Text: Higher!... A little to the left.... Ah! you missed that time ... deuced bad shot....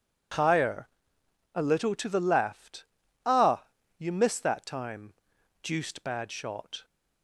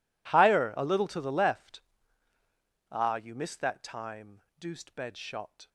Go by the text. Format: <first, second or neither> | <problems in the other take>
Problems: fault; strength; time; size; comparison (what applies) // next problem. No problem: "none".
first | says "bed" for "bad"; at 4.9 s